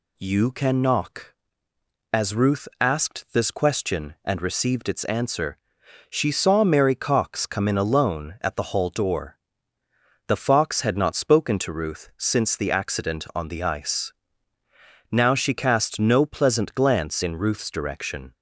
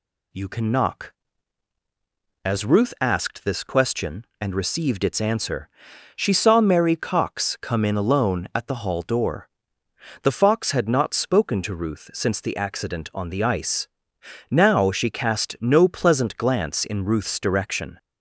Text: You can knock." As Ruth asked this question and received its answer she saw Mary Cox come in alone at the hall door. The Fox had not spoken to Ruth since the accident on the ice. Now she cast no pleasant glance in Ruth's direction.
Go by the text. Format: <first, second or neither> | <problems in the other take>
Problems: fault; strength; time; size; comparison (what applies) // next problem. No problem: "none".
neither | pauses between "answer" and "she"; noticeable; the same in both